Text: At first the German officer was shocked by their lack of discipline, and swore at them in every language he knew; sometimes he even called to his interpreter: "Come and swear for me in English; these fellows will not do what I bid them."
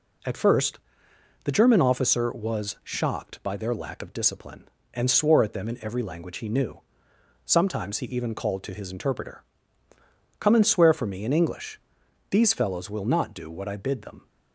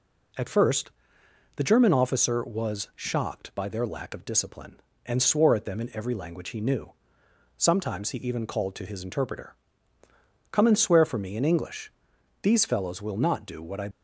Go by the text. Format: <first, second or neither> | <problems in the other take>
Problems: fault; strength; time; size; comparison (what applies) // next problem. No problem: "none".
first | pauses between "first" and "the"; noticeable; at 0.9 s; 0.66 s long; noticeable in the first // stops before "bid them"; at 13.9 s